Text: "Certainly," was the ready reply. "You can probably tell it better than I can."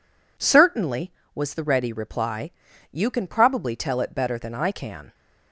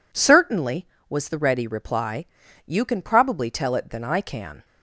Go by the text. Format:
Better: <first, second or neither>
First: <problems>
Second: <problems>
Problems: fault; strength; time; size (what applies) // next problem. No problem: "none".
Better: first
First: none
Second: skips "better"; at 3.8 s